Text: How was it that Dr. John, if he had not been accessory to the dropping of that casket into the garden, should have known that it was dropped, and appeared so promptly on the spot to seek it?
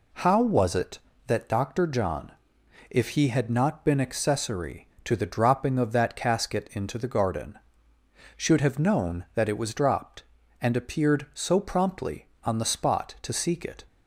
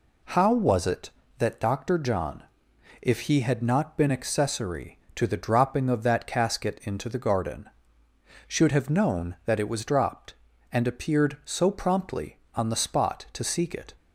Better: neither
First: none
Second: none

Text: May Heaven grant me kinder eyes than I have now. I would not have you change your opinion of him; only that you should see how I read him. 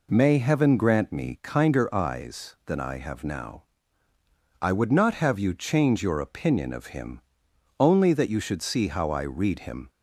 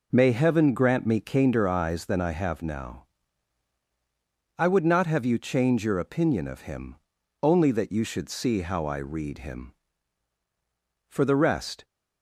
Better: first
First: none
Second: goes on to say "For the rest"; noticeable; from 11.0 s on; 0.76 s long

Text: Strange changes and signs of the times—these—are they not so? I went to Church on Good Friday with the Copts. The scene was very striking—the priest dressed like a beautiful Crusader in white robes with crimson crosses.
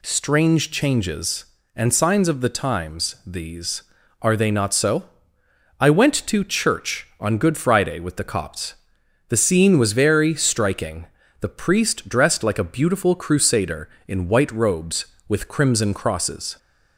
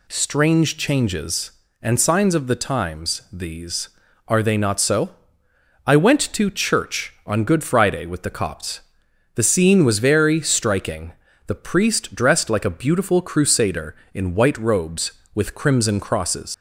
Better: first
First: none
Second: leaves "crosses" unfinished; at 16.5 s; 95 ms

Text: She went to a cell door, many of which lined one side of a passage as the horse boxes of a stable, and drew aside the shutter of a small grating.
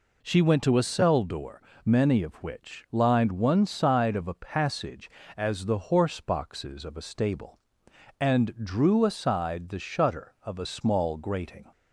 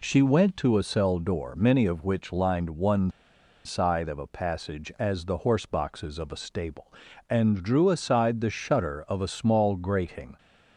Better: first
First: none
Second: pauses between "one" and "side"; noticeable; at 3.1 s; 0.54 s long

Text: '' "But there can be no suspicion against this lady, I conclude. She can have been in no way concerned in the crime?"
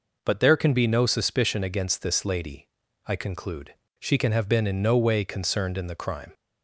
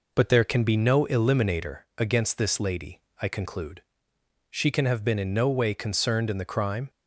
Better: first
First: none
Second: says "eliminator" for "suspicion"; at 1.0 s

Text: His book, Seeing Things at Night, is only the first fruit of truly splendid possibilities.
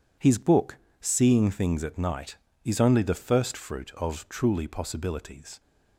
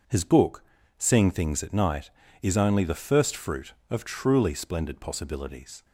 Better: second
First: skips "splendid"; at 4.6 s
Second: none

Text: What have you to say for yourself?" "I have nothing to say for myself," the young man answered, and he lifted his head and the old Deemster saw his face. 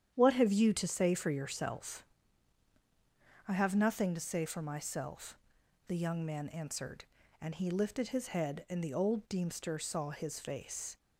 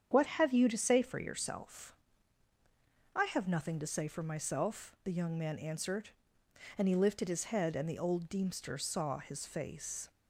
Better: neither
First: starts louder than the rest; strong; until 1.1 s; 9.5 dB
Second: starts louder than the rest; strong; until 1.1 s; 8 dB

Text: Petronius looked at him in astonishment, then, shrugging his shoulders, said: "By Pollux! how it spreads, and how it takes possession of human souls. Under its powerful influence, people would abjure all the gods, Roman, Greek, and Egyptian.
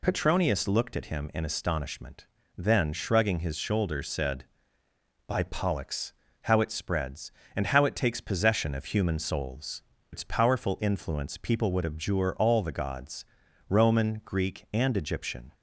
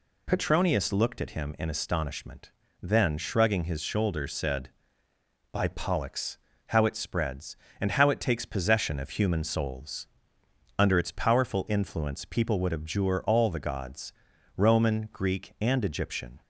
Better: second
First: skips "Under"; at 9.9 s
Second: none

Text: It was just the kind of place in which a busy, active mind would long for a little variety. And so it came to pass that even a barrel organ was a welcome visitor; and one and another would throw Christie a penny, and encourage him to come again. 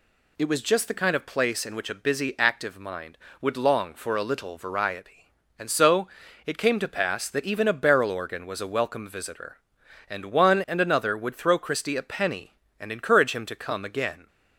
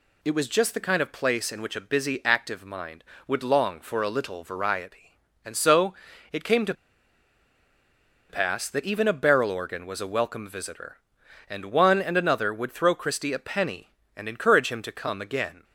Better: first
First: pauses between "so" and "it"; at 6.0 s; 0.38 s long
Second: pauses between "so" and "it"; at 5.9 s; 0.38 s long // pauses between "to" and "pass"; strong; at 6.7 s; 1.5 s long

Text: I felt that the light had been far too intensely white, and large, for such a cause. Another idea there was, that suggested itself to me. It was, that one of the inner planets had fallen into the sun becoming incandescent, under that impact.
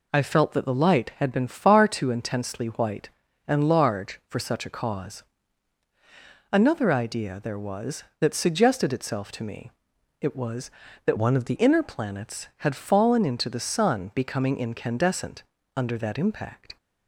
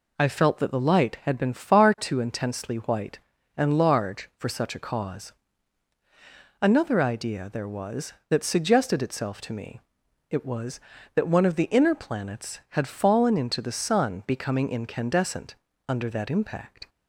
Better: second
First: changes voice from "one" to "the"; from 11.1 to 11.5 s; 0.4 s long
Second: none

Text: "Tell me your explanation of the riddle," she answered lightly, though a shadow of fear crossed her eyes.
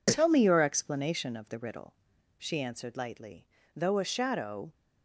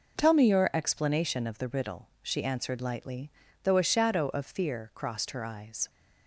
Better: second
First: stops before "of fear crossed her eyes"; at 4.7 s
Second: none

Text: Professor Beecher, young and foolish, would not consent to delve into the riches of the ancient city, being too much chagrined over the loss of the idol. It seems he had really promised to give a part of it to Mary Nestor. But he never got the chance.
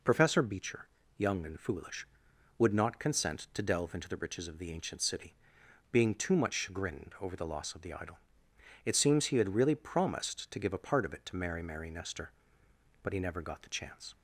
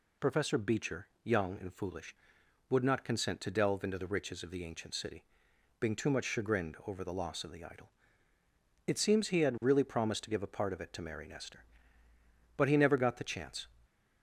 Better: second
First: says "Mary" twice; at 11.6 s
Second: none

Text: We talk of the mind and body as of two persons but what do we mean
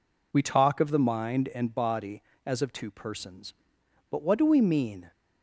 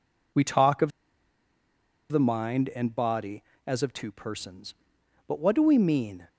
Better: first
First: none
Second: pauses between "of" and "the"; at 0.9 s; 1.2 s long

